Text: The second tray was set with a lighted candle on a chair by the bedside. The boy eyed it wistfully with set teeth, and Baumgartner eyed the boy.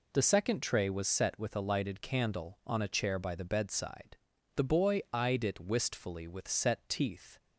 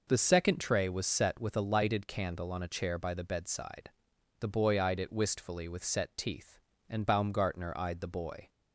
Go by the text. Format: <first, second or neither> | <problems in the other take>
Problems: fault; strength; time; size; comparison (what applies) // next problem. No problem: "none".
second | stops before "and Baumgartner eyed the boy"; at 7.3 s